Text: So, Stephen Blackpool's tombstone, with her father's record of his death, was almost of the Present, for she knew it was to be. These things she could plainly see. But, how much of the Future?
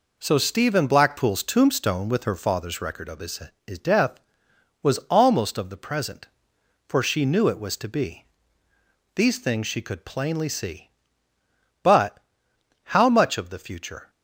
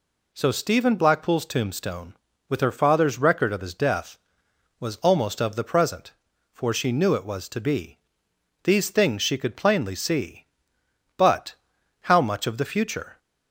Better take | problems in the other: second | says "his" twice; at 3.6 s

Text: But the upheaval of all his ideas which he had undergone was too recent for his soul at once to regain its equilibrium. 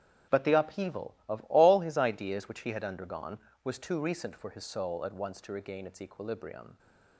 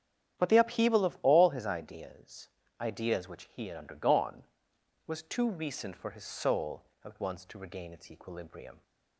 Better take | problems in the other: first | starts louder than the rest; strong; until 1.4 s; 10 dB; strong in the first // says "ideas" twice; at 2.7 s

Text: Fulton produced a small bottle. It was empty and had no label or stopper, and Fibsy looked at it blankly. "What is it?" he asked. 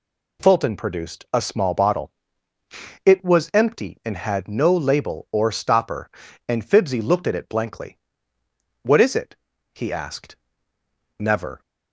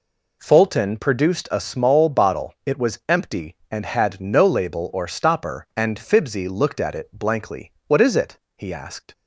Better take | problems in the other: second | goes on to say "Never"; slight; from 11.1 s on; 0.42 s long

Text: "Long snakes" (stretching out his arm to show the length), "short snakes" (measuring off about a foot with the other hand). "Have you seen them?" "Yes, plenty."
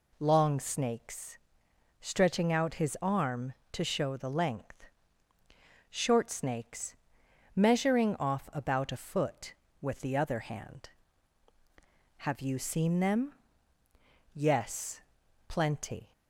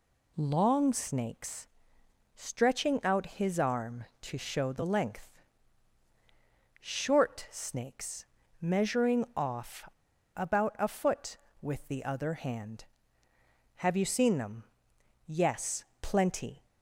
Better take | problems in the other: first | pauses between "off" and "about"; noticeable; at 9.8 s; 0.47 s long

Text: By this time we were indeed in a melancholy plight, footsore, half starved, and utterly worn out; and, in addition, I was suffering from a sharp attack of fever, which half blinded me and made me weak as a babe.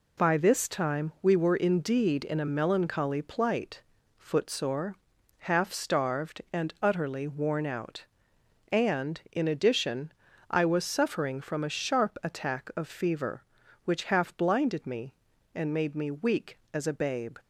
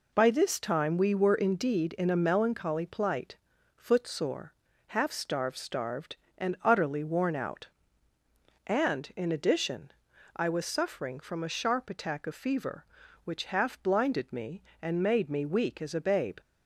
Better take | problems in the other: first | says "starved" twice; at 5.5 s

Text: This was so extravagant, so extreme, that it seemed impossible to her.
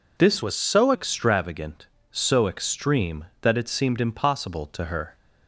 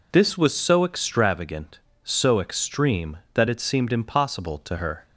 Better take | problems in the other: second | changes voice from "was" to "so"; from 0.4 to 0.9 s; 0.5 s long

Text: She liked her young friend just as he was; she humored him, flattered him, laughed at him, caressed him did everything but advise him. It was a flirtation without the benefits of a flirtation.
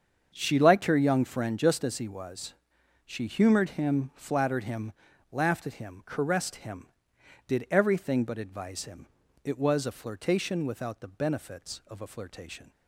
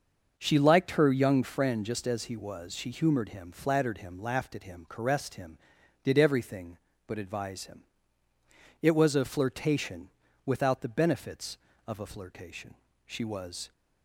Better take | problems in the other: first | starts louder than the rest; until 1.3 s; 6.5 dB; also in the first // pauses between "flirtation" and "without"; slight; at 10.0 s; 0.36 s long // goes on to say "She was"; noticeable; from 13.0 s on; 0.64 s long

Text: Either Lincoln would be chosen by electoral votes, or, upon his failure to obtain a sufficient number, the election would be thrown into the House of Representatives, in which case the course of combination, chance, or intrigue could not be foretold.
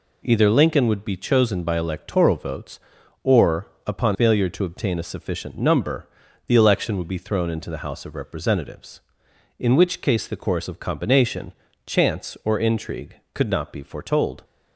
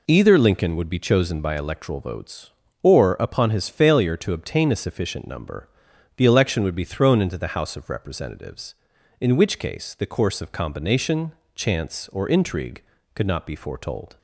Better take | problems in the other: second | skips "his"; at 4.1 s

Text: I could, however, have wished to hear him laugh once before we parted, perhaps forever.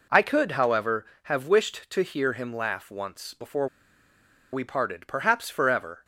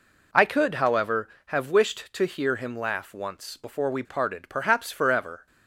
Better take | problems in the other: second | pauses between "before" and "we"; noticeable; at 3.6 s; 0.84 s long

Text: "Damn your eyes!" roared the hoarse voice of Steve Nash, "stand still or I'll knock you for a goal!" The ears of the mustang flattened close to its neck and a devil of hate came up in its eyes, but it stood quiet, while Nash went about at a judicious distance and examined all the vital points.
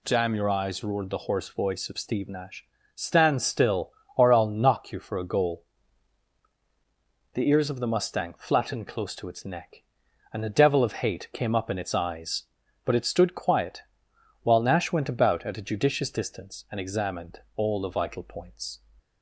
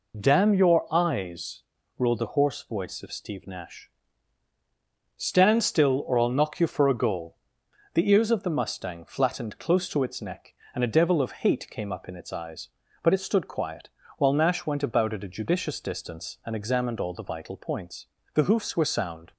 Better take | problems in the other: first | goes on to say "The hoofs were sound"; noticeable; from 18.3 s on; 0.98 s long

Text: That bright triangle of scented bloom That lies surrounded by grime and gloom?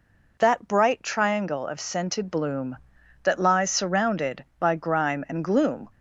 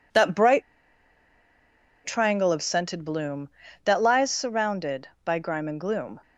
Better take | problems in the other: first | pauses between "bright" and "triangle"; strong; at 0.6 s; 1.4 s long

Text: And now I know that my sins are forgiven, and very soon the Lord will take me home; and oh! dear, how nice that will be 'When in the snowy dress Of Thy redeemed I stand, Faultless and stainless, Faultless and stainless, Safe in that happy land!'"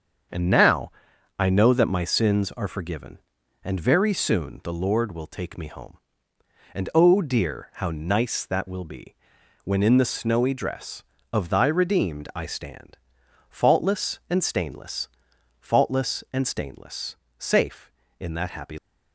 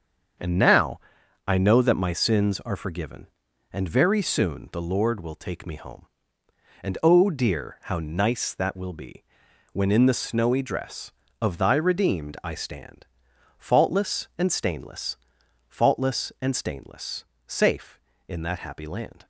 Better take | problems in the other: second | starts louder than the rest; until 1.7 s; 7 dB; also in the second // pauses between "now" and "I"; noticeable; at 0.9 s; 0.48 s long; noticeable in the second // pauses between "be" and "When"; noticeable; at 9.1 s; 0.48 s long; noticeable in the second // stops before "land"; at 18.7 s

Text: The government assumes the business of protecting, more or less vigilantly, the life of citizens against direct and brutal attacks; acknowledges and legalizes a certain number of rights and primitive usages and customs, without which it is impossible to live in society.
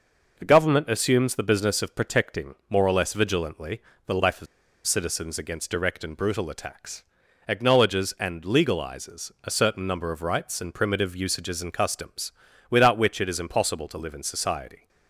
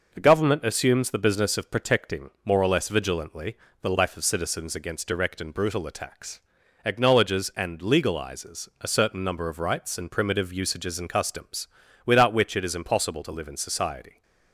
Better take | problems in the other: second | pauses between "of" and "citizens"; at 4.4 s; 0.40 s long

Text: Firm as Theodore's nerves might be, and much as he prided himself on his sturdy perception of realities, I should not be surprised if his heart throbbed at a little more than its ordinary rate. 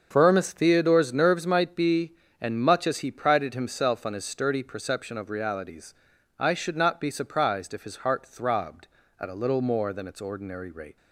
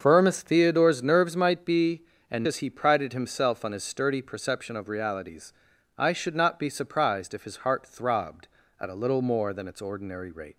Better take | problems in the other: first | starts louder than the rest; until 1.0 s; 6.5 dB; also in the first // skips "much"; at 2.4 s

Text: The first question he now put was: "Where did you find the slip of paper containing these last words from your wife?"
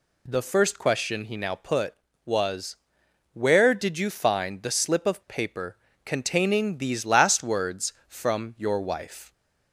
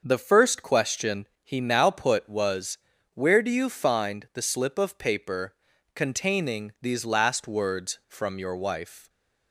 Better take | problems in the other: first | starts louder than the rest; until 1.0 s; 6 dB // pauses between "question" and "he"; slight; at 1.2 s; 0.16 s long // says "do" for "did"; at 3.4 s // pauses between "paper" and "containing"; at 5.5 s; 0.40 s long; slight in the first

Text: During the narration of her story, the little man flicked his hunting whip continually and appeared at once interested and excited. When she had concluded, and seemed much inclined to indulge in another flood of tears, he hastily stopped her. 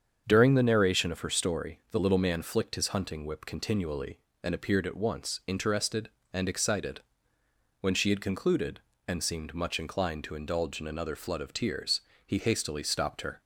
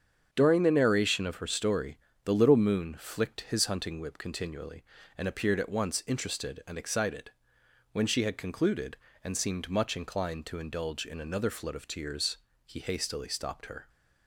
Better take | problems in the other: first | starts louder than the rest; strong; until 1.3 s; 7.5 dB; strong in the first // says "moon" for "man"; at 2.5 s

